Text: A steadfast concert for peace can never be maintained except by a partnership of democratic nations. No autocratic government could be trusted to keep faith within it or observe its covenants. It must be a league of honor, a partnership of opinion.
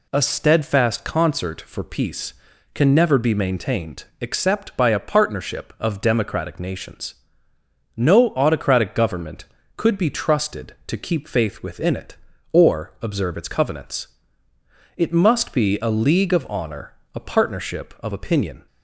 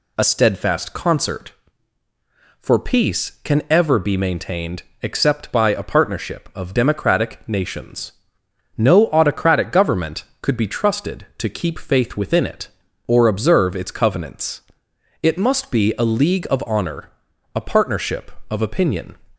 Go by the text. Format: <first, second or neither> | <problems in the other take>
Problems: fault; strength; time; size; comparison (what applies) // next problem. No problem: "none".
first | says "ever" for "never"; at 3.6 s // pauses between "maintained" and "except"; slight; at 4.8 s; 0.18 s long; slight in the first